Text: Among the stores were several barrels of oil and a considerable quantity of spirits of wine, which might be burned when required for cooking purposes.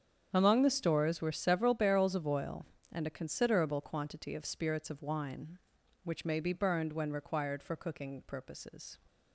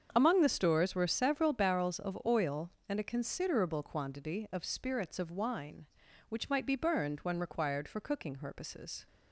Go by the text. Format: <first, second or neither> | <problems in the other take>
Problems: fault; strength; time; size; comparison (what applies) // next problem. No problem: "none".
second | starts louder than the rest; strong; until 1.3 s; 8 dB; strong in the second // says "may" for "might"; at 6.2 s